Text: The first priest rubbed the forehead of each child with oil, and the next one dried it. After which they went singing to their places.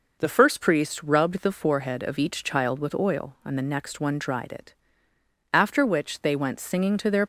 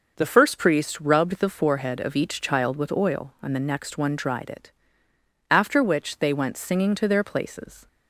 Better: second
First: stops before "places"; at 7.2 s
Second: none

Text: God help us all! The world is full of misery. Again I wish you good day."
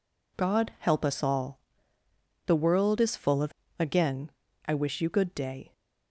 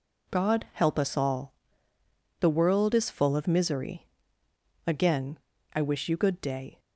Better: second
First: skips "misery"; at 3.6 s // pauses between "Again" and "I"; slight; at 4.3 s; 0.36 s long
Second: pauses between "Again" and "I"; slight; at 5.3 s; 0.36 s long

